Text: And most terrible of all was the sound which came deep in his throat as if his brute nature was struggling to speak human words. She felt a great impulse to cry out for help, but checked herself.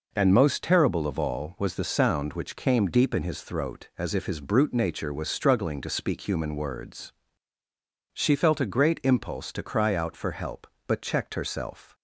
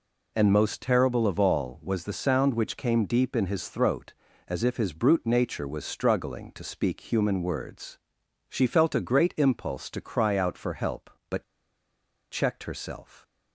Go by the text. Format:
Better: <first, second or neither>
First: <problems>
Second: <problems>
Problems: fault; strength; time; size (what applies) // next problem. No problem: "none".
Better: first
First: none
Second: pauses between "but" and "checked"; noticeable; at 11.4 s; 0.88 s long